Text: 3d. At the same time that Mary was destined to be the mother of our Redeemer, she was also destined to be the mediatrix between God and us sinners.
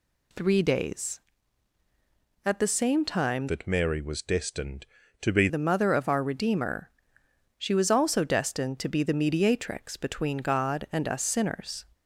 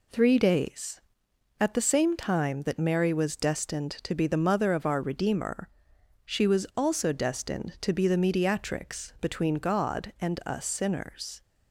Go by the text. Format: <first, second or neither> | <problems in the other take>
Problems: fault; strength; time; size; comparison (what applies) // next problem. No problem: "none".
second | changes voice from "that" to "be"; from 3.4 to 5.4 s; 2.0 s long